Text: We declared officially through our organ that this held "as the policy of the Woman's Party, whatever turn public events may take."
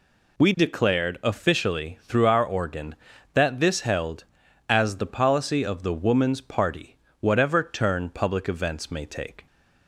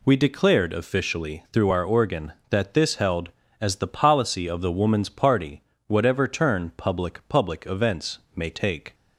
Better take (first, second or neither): first